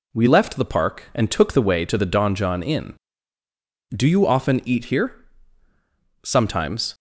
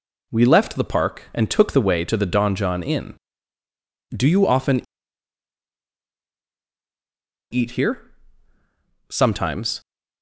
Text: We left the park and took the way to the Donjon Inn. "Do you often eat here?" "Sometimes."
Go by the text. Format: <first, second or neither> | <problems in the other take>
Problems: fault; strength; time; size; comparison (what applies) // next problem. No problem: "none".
first | pauses between "often" and "eat"; strong; at 4.8 s; 2.7 s long